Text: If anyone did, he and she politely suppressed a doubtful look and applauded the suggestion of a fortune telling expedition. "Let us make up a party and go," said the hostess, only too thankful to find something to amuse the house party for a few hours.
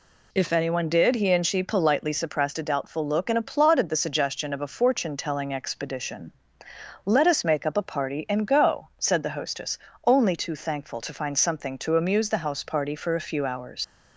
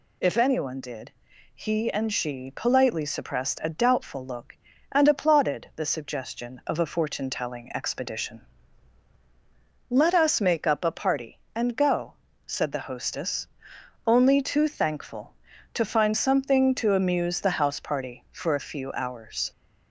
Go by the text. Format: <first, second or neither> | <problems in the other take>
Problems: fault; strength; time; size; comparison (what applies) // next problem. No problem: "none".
second | leaves "hours" unfinished; at 13.8 s; 90 ms